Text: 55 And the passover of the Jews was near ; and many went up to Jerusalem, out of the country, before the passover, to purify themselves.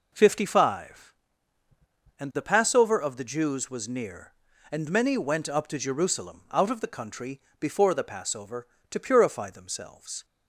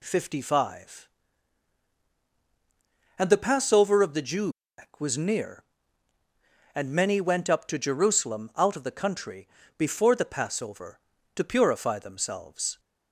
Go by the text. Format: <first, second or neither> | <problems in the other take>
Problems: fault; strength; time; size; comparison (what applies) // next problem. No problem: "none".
neither | none